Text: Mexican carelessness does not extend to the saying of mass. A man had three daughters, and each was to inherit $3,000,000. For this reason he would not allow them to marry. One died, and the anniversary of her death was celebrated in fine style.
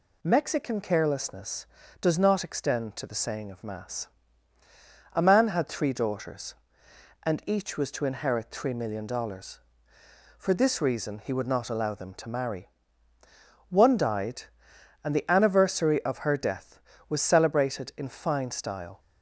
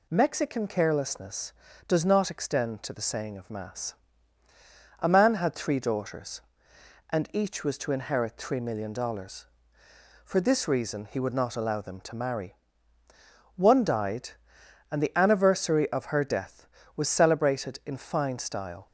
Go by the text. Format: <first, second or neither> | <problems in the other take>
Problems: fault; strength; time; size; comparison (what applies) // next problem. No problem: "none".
neither | none